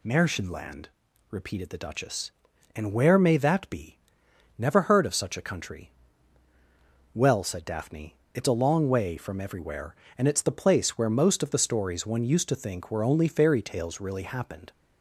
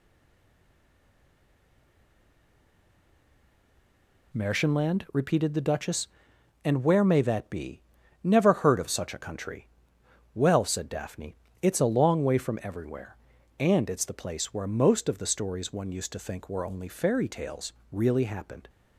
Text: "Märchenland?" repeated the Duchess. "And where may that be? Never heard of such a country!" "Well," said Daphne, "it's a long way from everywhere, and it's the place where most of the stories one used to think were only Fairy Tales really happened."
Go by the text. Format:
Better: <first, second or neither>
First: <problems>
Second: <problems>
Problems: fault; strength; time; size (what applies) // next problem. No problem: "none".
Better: first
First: none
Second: stays silent before the first word; strong; until 4.3 s; 4.3 s long // pauses between "Tales" and "really"; slight; at 17.7 s; 0.18 s long